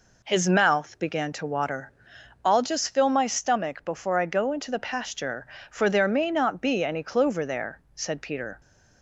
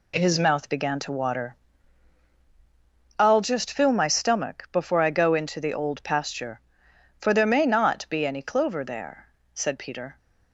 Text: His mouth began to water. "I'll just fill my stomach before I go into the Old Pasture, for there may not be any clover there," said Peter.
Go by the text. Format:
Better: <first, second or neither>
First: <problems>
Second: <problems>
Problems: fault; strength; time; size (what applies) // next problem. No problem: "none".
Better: second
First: skips "Old"; at 4.7 s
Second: none